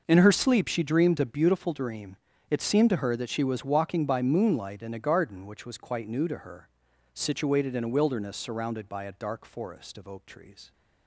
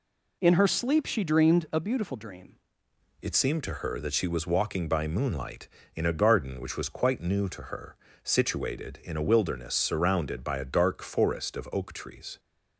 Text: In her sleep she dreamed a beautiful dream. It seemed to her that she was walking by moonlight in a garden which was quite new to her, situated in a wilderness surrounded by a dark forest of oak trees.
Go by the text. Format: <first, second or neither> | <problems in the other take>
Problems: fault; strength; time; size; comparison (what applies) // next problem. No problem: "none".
first | changes voice at "It"; from 3.2 s on; 9.1 s long